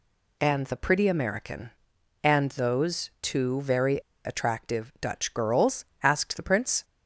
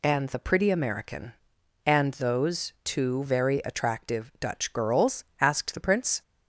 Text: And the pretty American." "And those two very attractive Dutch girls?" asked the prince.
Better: second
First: pauses between "very" and "attractive"; slight; at 3.9 s; 0.28 s long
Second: none

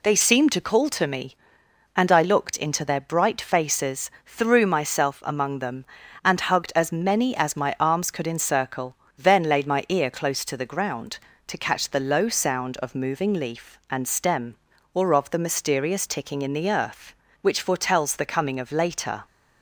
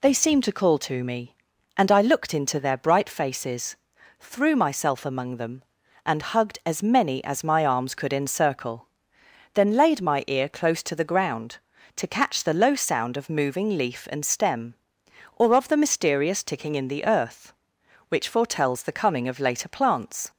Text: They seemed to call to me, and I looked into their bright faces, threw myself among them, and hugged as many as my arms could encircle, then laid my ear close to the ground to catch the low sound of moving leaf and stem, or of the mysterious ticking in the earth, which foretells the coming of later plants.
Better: second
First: stops before "plants"; at 19.2 s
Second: none

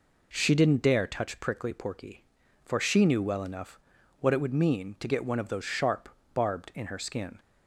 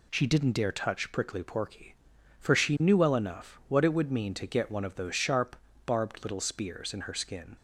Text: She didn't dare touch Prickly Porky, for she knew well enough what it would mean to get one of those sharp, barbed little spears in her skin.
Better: second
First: pauses between "enough" and "what"; at 3.7 s; 0.44 s long // skips "little spears"; at 6.7 s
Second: none

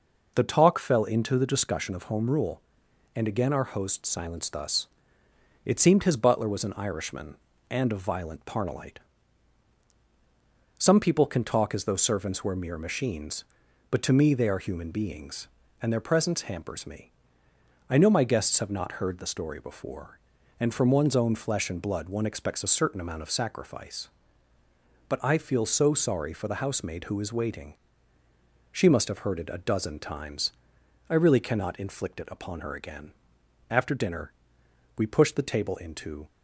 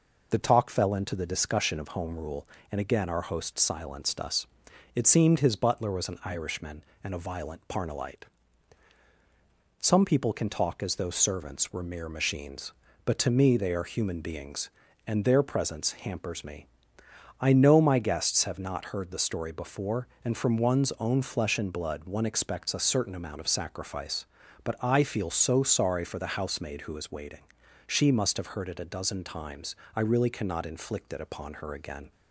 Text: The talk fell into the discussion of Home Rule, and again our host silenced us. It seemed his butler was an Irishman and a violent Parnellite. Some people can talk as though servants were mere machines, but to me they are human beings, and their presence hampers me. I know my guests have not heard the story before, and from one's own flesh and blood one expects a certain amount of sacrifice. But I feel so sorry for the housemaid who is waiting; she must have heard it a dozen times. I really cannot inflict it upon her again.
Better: second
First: goes on to say "After dinner we pushed the table into"; strong; from 33.7 s on; 2.5 s long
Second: none

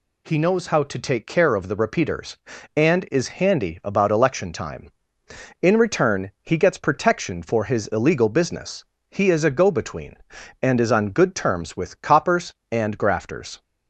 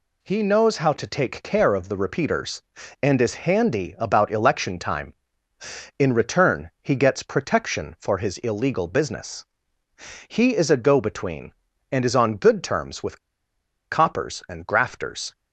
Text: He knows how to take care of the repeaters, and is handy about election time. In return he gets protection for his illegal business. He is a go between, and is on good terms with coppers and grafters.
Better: first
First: none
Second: pauses between "with" and "coppers"; noticeable; at 13.1 s; 0.72 s long

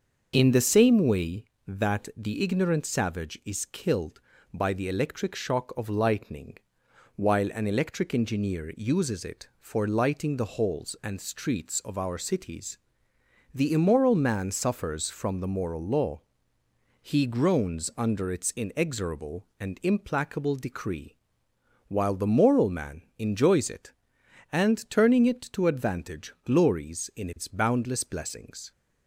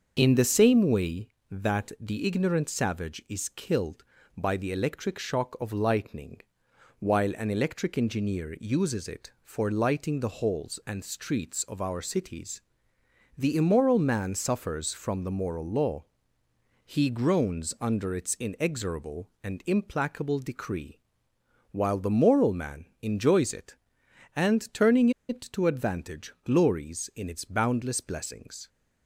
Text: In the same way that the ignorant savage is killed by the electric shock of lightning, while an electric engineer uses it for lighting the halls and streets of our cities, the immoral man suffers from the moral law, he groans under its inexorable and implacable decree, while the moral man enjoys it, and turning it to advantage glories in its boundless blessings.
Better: first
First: starts louder than the rest; until 1.3 s; 6.5 dB // pauses between "man" and "enjoys"; slight; at 23.0 s; 0.16 s long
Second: starts louder than the rest; until 1.1 s; 6.5 dB // pauses between "man" and "enjoys"; slight; at 22.8 s; 0.16 s long // pauses between "turning" and "it"; slight; at 25.0 s; 0.19 s long

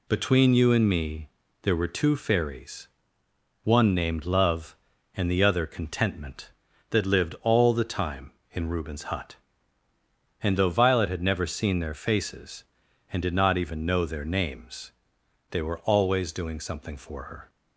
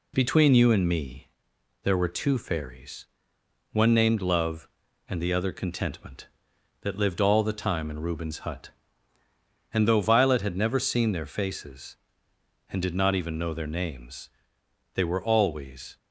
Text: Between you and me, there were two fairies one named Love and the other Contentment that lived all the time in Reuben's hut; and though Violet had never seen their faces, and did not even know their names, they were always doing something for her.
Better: first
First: pauses between "fairies" and "one"; noticeable; at 2.8 s; 0.74 s long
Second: pauses between "fairies" and "one"; noticeable; at 3.0 s; 0.66 s long // stops before "doing something for her"; at 15.9 s

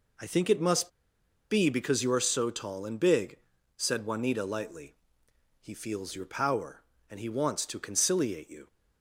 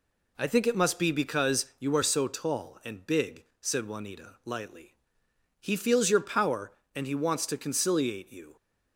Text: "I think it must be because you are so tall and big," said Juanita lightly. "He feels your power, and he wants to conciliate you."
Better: second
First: pauses between "must" and "be"; noticeable; at 0.8 s; 0.61 s long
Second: none

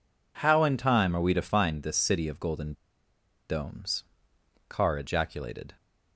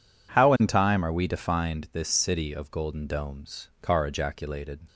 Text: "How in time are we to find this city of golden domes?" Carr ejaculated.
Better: second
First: pauses between "golden" and "domes"; noticeable; at 2.7 s; 0.75 s long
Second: none

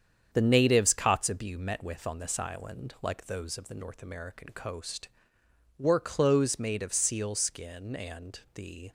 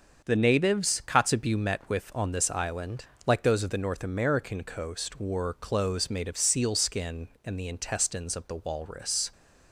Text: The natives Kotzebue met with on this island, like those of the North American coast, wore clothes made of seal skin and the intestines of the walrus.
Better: second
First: starts louder than the rest; strong; until 1.3 s; 8 dB // pauses between "and" and "the"; slight; at 8.3 s; 0.16 s long // stops before "intestines of the walrus"; at 8.8 s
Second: starts louder than the rest; until 1.2 s; 6.5 dB

